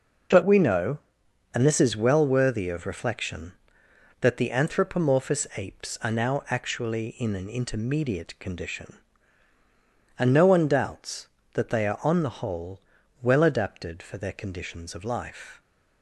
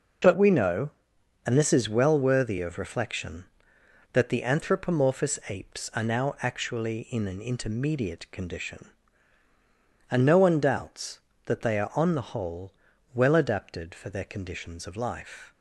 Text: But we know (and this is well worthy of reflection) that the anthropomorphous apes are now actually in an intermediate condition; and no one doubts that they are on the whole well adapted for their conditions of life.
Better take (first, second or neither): neither